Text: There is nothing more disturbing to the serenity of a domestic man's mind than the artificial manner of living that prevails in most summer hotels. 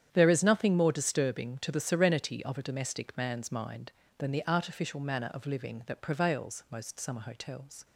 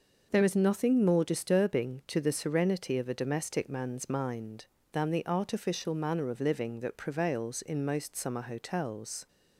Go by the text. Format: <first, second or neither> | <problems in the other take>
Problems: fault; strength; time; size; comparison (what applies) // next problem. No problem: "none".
second | starts louder than the rest; strong; until 1.1 s; 9.5 dB // skips "in"; at 6.6 s